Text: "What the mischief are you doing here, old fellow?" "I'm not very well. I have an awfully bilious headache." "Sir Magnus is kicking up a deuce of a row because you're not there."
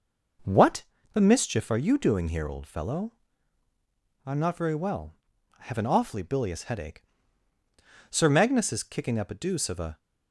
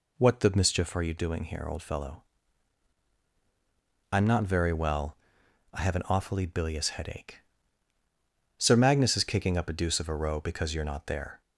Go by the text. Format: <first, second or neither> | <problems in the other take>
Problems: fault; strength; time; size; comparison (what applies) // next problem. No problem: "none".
second | pauses between "What" and "the"; slight; at 0.8 s; 0.28 s long // stops before "row because you're not there"; at 9.9 s